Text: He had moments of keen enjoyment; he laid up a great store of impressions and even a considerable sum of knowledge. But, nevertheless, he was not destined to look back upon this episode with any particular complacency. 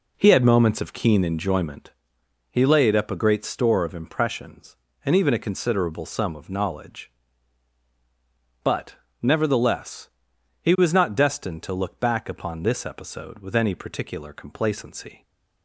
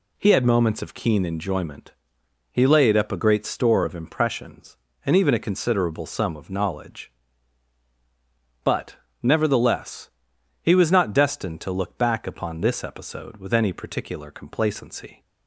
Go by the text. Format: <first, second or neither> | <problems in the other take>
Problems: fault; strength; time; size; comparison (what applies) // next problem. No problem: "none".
second | starts louder than the rest; until 2.0 s; 3.5 dB